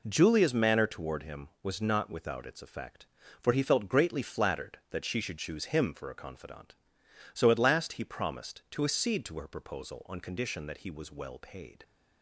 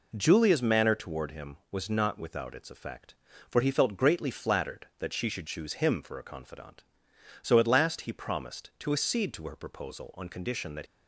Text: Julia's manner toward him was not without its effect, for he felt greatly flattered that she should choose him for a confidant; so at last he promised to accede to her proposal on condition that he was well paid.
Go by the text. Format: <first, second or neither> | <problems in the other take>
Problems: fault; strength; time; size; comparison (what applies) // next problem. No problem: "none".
first | stops before "he was well paid"; at 10.8 s